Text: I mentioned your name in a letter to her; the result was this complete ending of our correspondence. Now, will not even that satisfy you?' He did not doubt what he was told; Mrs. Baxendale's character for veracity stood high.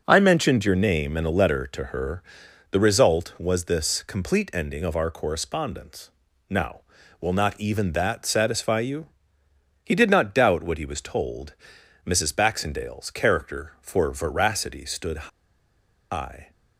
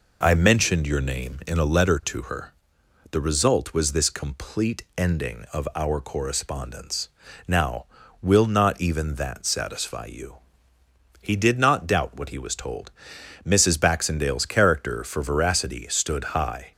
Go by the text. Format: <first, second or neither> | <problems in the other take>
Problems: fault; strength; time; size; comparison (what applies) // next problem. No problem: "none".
second | pauses between "stood" and "high"; noticeable; at 15.2 s; 0.82 s long